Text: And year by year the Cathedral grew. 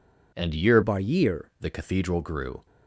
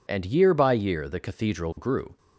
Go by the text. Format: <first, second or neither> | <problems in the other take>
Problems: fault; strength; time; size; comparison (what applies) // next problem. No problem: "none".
second | changes voice from "by" to "year"; from 0.8 to 1.5 s; 0.7 s long